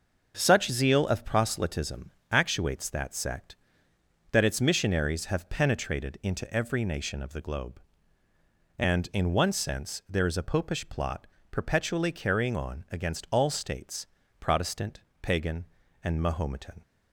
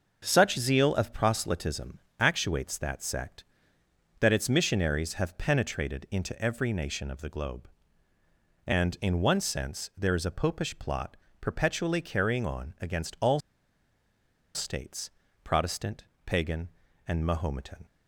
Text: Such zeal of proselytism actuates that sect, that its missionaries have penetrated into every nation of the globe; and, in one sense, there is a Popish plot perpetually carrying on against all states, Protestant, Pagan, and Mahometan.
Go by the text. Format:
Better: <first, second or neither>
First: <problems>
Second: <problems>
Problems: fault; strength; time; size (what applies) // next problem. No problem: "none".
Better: first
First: starts louder than the rest; until 1.4 s; 6.5 dB // pauses between "proselytism" and "actuates"; slight; at 2.1 s; 0.18 s long // pauses between "plot" and "perpetually"; slight; at 11.2 s; 0.24 s long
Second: starts louder than the rest; noticeable; until 1.2 s; 6 dB // pauses between "proselytism" and "actuates"; slight; at 1.9 s; 0.18 s long // pauses between "plot" and "perpetually"; slight; at 11.1 s; 0.24 s long // pauses between "all" and "states"; at 13.4 s; 1.1 s long